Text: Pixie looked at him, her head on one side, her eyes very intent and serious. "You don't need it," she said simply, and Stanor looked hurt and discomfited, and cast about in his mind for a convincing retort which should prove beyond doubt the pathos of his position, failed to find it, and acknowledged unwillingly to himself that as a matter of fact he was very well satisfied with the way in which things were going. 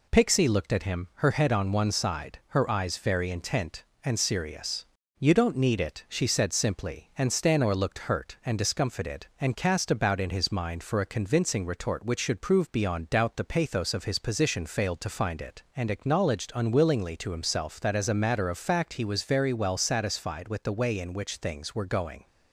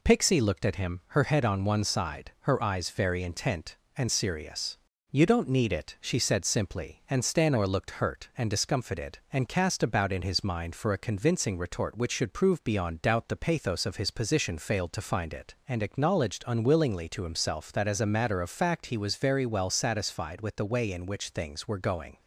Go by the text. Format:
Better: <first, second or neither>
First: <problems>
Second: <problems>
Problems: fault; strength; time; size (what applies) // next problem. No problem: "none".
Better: neither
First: none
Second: none